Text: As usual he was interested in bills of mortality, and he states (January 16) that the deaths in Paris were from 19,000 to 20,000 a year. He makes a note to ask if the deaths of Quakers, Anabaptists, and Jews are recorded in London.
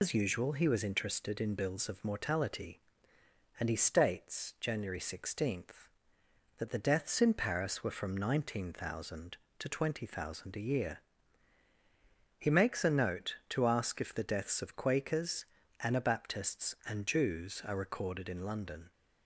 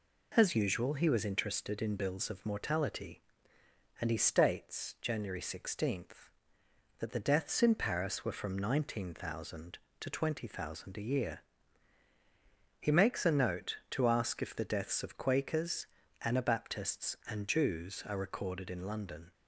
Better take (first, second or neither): second